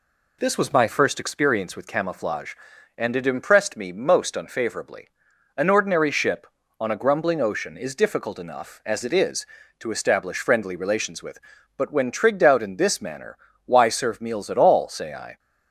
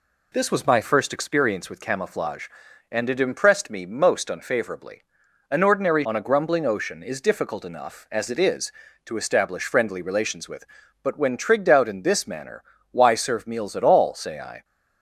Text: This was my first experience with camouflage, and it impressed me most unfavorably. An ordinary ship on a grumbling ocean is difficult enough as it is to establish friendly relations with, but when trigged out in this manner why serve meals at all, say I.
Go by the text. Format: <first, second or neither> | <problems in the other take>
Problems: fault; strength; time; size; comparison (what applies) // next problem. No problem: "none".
first | skips "ship"; at 6.0 s // pauses between "manner" and "why"; slight; at 12.6 s; 0.28 s long; slight in the first